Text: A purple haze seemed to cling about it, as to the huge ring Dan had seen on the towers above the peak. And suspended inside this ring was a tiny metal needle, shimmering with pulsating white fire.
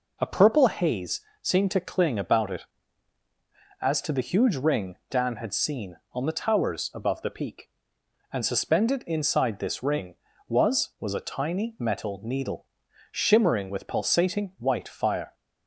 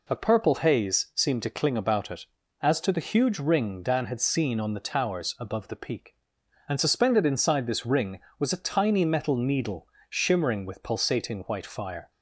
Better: second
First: pauses between "haze" and "seemed"; slight; at 1.2 s; 0.20 s long // says "was" twice; at 10.9 s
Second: none

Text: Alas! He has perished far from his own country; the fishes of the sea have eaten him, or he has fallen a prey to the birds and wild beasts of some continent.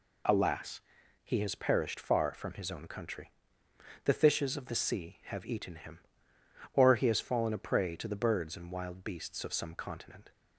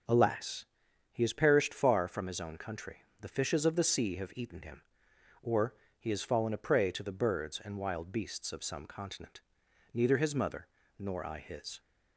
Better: first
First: none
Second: starts louder than the rest; noticeable; until 1.5 s; 6 dB // pauses between "or" and "he"; slight; at 5.7 s; 0.24 s long // goes on to say "Neither his mother nor I his"; strong; from 9.9 s on; 1.8 s long

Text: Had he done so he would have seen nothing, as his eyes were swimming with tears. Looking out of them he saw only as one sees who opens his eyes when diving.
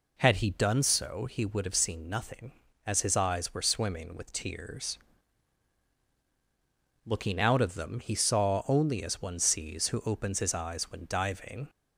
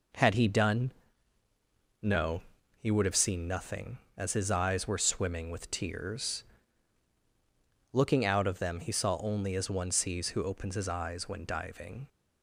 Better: first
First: none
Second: says "no" for "so"; at 2.0 s

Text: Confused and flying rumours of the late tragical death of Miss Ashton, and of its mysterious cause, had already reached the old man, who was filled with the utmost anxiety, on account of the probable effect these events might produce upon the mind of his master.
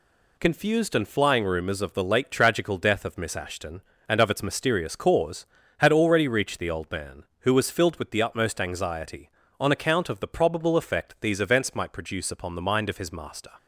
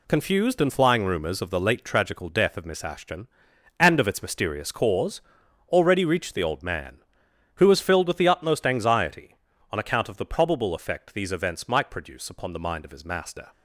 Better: first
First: none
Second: skips "had"; at 5.4 s

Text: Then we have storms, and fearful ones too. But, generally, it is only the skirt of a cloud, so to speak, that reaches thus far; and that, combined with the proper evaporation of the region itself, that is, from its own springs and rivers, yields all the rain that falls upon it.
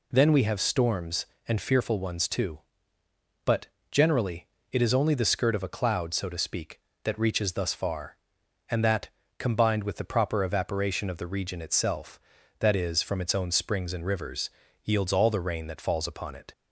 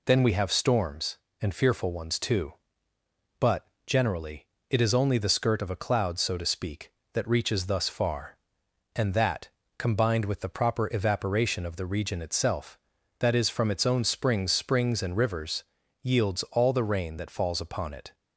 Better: first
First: none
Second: says "springs" twice; at 14.5 s

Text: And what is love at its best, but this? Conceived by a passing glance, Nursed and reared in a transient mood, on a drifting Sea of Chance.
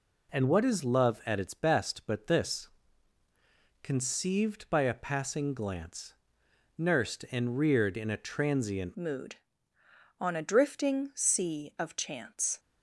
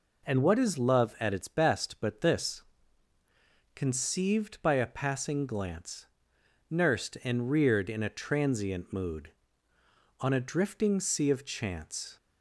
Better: second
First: changes voice at "mood"; from 8.9 s on; 3.6 s long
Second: none

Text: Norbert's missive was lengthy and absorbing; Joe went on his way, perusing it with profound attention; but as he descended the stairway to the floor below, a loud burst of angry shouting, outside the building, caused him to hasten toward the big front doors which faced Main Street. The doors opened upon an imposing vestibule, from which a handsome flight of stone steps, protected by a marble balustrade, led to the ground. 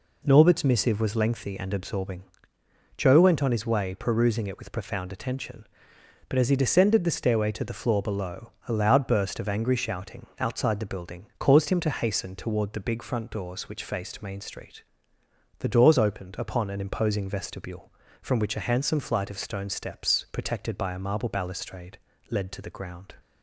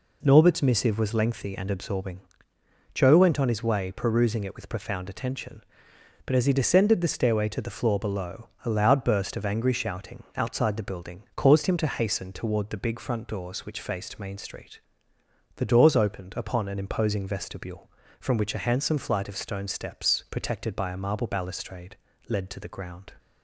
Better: neither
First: none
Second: none

